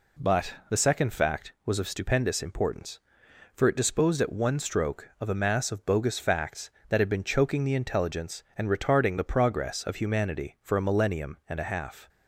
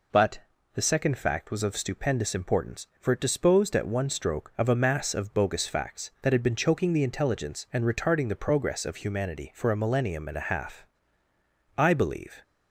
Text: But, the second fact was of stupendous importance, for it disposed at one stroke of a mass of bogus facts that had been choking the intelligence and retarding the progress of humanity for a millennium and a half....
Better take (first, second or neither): first